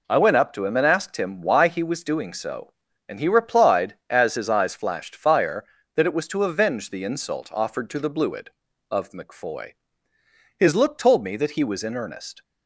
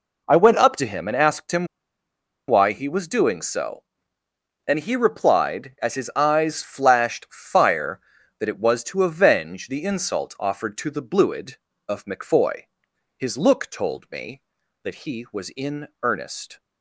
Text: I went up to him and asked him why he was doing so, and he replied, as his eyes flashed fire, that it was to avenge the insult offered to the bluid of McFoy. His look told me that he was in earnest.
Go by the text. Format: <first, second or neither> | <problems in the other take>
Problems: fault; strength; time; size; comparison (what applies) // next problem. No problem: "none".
first | pauses between "him" and "why"; noticeable; at 1.6 s; 0.82 s long